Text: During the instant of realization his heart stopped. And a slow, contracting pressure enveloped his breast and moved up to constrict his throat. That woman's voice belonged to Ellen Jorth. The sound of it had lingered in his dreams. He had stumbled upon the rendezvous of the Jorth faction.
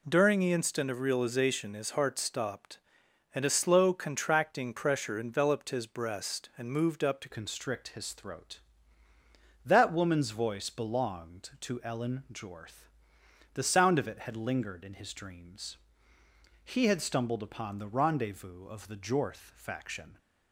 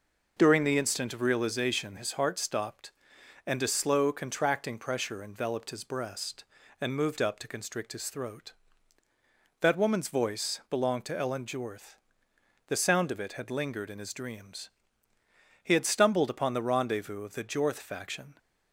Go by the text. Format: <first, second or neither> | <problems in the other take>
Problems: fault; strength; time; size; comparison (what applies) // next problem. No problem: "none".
second | changes voice at "constrict"; from 7.3 s on; 12.8 s long